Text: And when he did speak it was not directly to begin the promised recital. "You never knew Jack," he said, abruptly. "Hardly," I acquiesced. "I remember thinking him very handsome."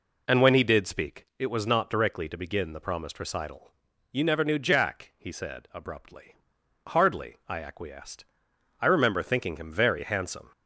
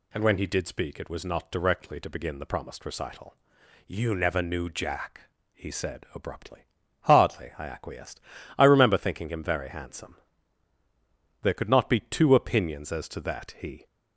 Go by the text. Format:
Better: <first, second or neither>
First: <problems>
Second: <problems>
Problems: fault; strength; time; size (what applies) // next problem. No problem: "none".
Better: first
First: none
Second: goes on to say "There could not be two opinions as to that he"; strong; from 11.4 s on; 2.4 s long